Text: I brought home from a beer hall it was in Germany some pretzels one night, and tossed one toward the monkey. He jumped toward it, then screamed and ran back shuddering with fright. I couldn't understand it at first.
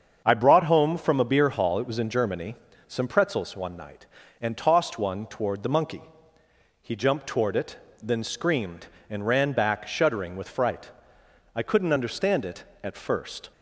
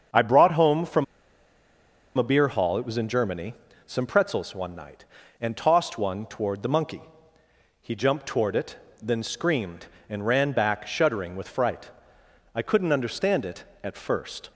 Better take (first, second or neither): first